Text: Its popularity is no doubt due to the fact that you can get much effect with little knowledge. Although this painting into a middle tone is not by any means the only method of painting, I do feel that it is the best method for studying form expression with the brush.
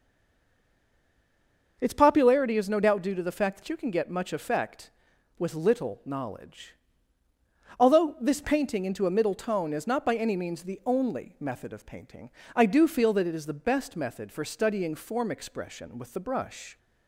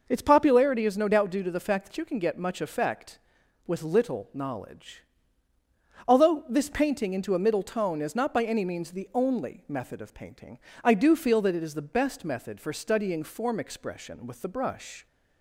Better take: second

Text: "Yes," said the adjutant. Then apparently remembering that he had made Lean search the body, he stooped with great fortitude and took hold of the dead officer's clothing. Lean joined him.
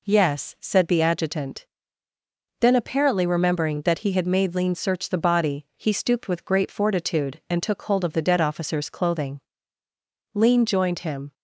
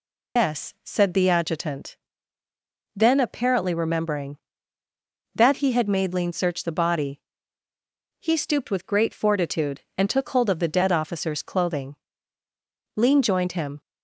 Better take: first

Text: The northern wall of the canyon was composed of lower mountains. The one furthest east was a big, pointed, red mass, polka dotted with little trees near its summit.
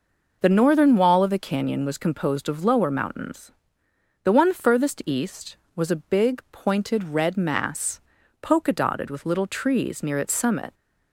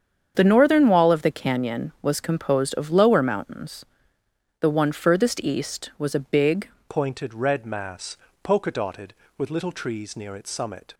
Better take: first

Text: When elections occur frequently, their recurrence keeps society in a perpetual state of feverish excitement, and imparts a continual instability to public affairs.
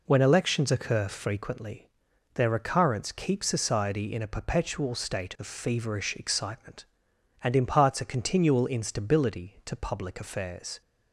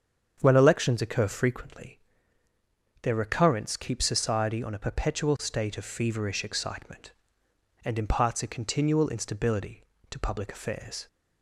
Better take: first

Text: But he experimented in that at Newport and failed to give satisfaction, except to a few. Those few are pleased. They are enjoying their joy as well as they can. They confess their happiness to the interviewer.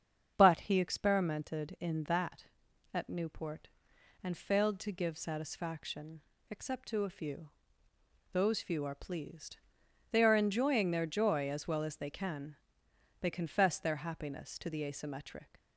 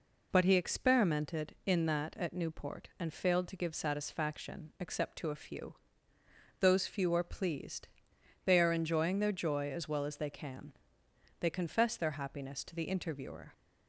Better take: second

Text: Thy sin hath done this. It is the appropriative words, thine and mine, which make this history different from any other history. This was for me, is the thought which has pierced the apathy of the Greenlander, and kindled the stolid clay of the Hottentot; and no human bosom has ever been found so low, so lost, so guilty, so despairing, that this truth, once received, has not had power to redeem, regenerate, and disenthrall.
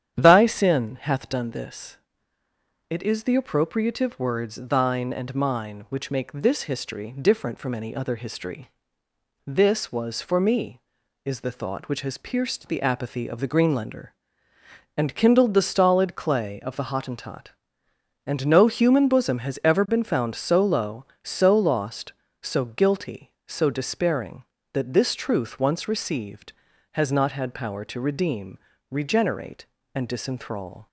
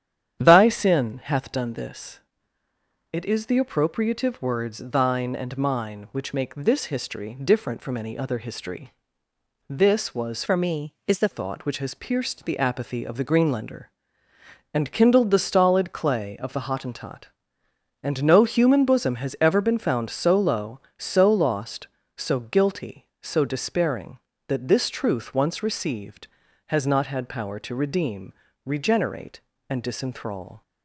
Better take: first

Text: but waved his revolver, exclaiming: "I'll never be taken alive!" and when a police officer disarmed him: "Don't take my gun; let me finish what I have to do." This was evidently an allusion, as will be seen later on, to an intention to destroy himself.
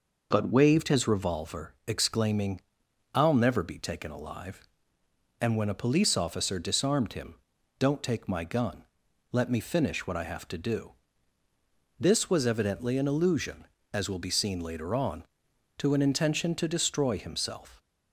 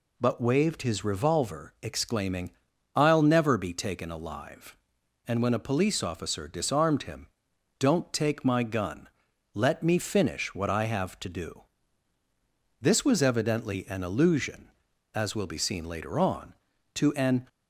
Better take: first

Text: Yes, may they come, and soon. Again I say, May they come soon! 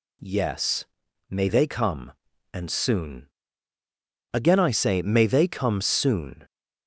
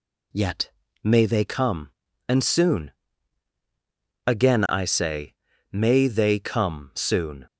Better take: first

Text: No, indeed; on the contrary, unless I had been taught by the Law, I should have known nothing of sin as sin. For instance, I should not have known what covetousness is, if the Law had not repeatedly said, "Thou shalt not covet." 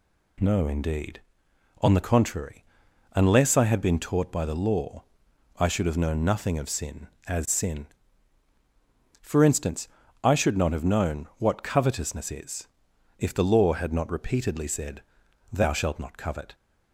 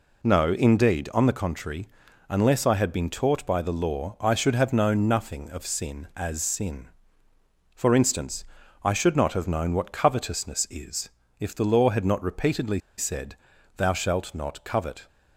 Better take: first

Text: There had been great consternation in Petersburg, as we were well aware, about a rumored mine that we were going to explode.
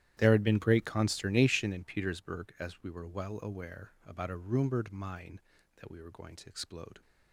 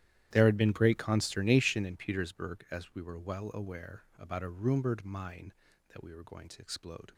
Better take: neither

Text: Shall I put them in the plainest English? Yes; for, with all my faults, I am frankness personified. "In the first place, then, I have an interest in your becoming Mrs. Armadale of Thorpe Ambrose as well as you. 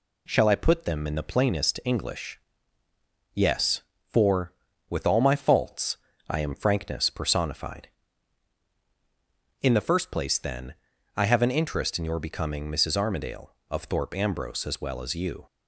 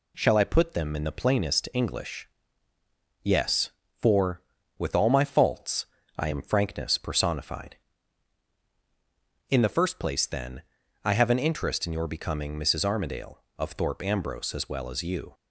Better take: neither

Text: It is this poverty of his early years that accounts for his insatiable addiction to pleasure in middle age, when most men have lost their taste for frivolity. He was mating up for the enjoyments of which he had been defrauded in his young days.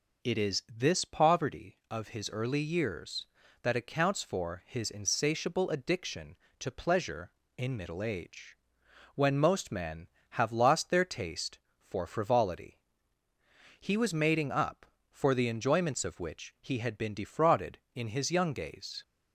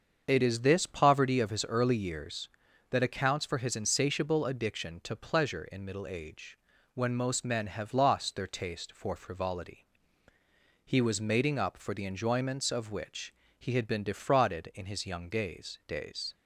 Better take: first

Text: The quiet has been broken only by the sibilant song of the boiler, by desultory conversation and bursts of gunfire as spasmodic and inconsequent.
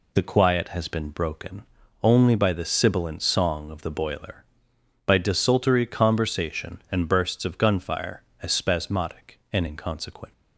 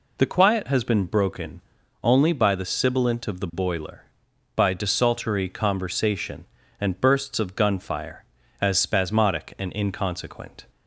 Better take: first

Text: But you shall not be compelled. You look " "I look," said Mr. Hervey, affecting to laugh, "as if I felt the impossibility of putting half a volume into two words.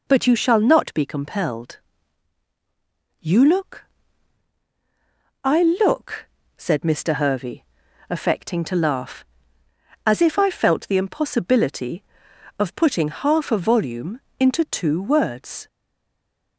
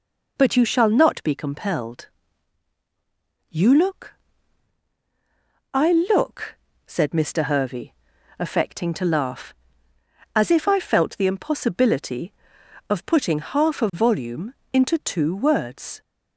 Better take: second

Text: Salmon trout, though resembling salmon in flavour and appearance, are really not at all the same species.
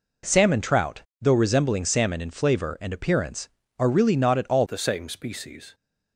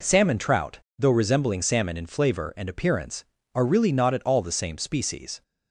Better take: second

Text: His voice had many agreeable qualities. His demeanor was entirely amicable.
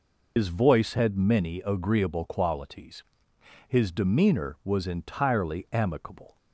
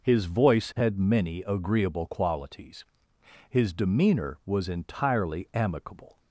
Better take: second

